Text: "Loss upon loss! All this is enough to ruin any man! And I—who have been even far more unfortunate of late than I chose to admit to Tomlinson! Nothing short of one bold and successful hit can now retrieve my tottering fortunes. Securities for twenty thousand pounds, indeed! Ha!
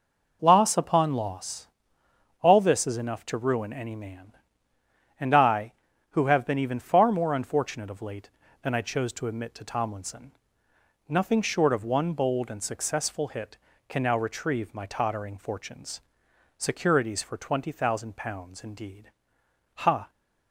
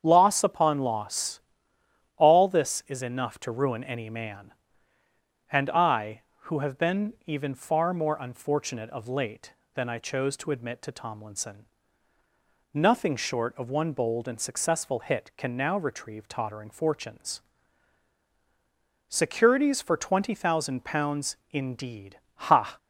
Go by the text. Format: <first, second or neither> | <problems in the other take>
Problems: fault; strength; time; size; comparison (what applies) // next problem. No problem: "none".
first | starts louder than the rest; strong; until 1.0 s; 8 dB // skips "my"; at 16.2 s